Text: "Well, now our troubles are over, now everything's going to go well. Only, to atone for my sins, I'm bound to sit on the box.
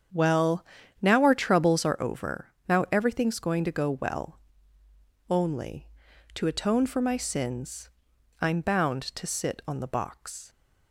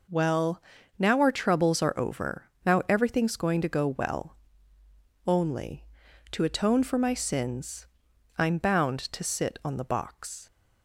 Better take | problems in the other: second | starts louder than the rest; strong; until 1.9 s; 8 dB

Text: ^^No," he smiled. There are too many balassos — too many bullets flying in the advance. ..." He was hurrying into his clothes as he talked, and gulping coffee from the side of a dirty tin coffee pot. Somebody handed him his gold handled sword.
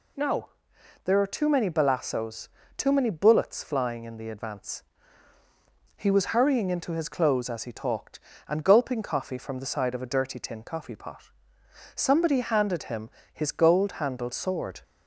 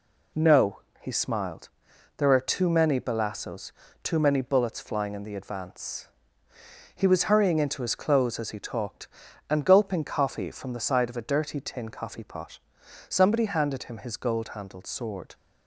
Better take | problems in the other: second | skips "he smiled"; at 0.7 s // pauses between "him" and "his"; slight; at 13.1 s; 0.20 s long

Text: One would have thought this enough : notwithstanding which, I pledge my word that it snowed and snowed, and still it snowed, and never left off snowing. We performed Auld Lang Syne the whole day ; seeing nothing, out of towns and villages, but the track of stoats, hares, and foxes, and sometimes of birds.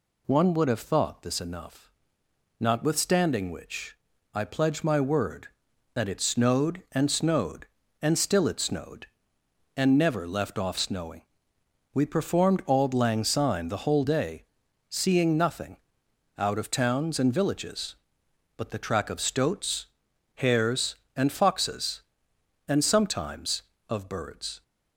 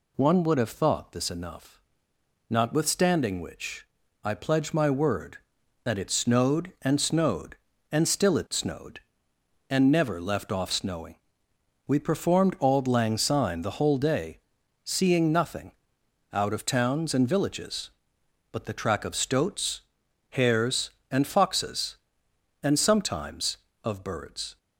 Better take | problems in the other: neither | none

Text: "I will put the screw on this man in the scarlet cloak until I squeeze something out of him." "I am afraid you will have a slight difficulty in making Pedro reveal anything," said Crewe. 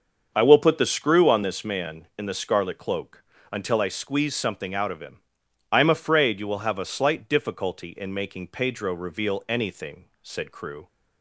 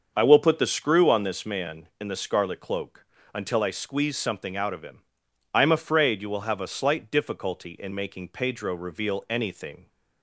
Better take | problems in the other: first | starts louder than the rest; until 1.1 s; 6.5 dB; also in the first // pauses between "cloak" and "until"; slight; at 3.0 s; 0.28 s long; slight in the first // stops before "said Crewe"; at 9.8 s

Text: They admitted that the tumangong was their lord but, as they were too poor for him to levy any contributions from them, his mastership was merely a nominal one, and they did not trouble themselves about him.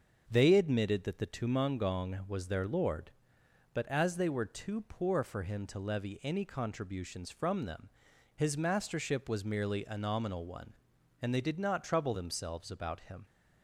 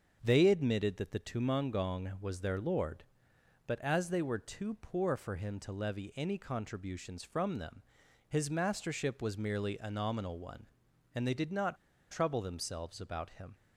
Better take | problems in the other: first | starts louder than the rest; until 1.2 s; 6.5 dB; also in the first // pauses between "not" and "trouble"; slight; at 11.7 s; 0.34 s long

